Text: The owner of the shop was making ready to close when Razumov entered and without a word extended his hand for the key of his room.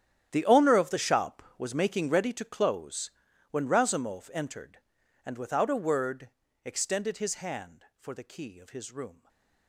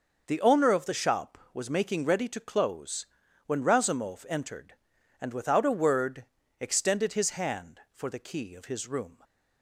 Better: second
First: gets quieter; strong; throughout; 16.5 dB // pauses between "close" and "when"; at 3.0 s; 0.40 s long // pauses between "word" and "extended"; at 6.2 s; 0.38 s long // stays silent after the last word; slight; from 9.1 s on; 0.5 s long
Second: pauses between "close" and "when"; at 3.0 s; 0.40 s long // pauses between "word" and "extended"; at 6.2 s; 0.38 s long

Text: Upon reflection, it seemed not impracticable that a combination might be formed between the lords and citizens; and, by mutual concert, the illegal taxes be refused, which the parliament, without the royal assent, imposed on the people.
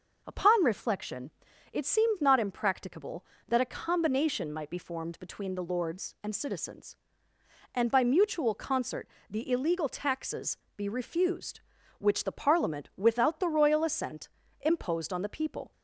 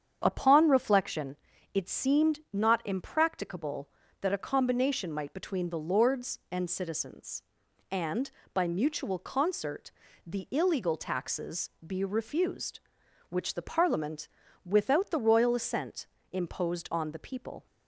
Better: first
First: pauses between "taxes" and "be"; slight; at 10.5 s; 0.18 s long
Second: starts louder than the rest; strong; until 1.2 s; 8 dB // skips "be formed"; at 5.3 s // pauses between "taxes" and "be"; slight; at 11.6 s; 0.18 s long

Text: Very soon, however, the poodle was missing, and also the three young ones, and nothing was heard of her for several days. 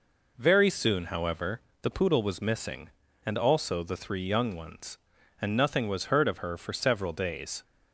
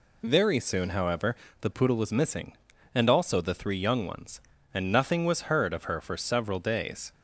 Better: neither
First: none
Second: none

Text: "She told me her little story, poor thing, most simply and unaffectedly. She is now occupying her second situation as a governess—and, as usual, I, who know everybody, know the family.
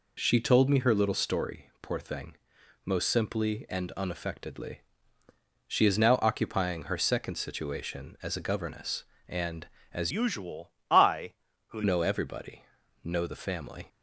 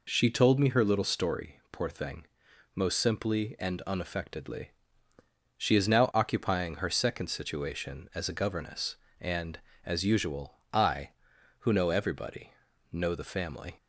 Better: second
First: changes voice from "usual" to "who"; from 10.1 to 11.8 s; 1.7 s long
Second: none

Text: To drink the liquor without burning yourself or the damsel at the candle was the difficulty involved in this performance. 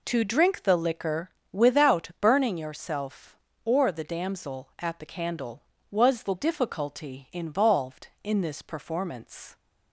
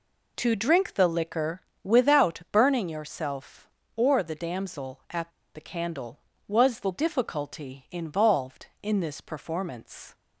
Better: first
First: pauses between "liquor" and "without"; slight; at 1.3 s; 0.22 s long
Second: pauses between "liquor" and "without"; slight; at 1.6 s; 0.22 s long // pauses between "at" and "the"; slight; at 5.3 s; 0.24 s long

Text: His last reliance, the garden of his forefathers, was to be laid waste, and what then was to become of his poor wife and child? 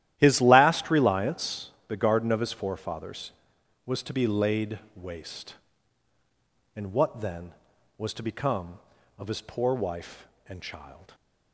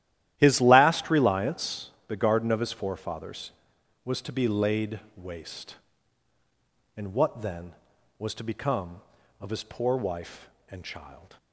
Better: neither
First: starts louder than the rest; strong; until 1.1 s; 12.5 dB // pauses between "laid" and "waste"; slight; at 4.7 s; 0.16 s long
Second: starts louder than the rest; strong; until 1.3 s; 13 dB // pauses between "laid" and "waste"; slight; at 4.9 s; 0.16 s long

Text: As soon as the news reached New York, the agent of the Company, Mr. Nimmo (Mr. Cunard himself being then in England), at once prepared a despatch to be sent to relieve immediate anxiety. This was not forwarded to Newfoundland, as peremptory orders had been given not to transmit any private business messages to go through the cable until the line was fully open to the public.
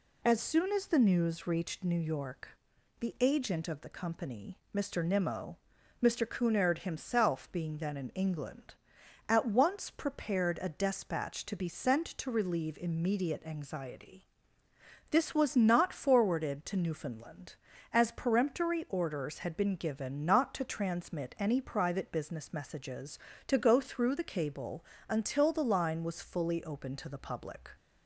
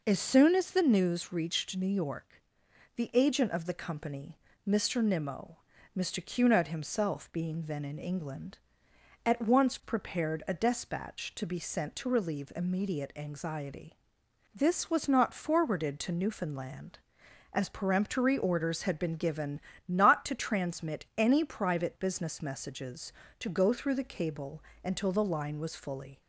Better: first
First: pauses between "cable" and "until"; slight; at 24.8 s; 0.24 s long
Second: pauses between "given" and "not"; slight; at 19.5 s; 0.30 s long // pauses between "cable" and "until"; slight; at 24.6 s; 0.22 s long // stops before "open to the public"; at 26.2 s

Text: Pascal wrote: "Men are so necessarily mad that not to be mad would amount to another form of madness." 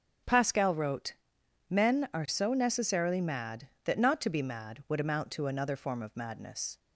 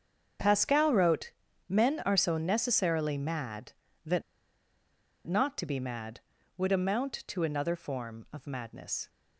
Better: first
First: starts louder than the rest; until 1.8 s; 7 dB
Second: starts louder than the rest; strong; until 1.7 s; 7 dB // pauses between "that" and "not"; at 4.2 s; 1.0 s long

